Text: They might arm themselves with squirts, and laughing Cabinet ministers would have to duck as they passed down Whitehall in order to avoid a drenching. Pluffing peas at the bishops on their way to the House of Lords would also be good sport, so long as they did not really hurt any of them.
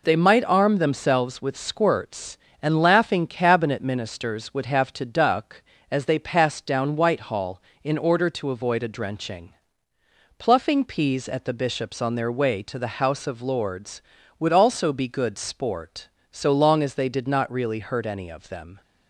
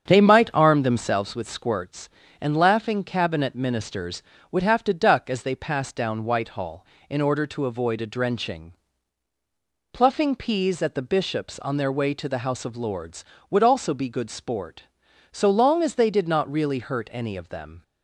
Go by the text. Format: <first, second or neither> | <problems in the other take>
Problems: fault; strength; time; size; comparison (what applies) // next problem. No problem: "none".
first | starts louder than the rest; strong; until 1.3 s; 7.5 dB